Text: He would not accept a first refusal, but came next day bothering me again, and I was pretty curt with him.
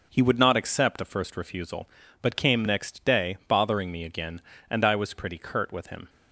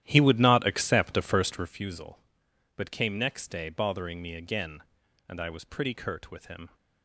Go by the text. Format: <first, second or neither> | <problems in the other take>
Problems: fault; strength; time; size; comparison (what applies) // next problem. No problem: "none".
first | starts louder than the rest; strong; until 1.8 s; 12.5 dB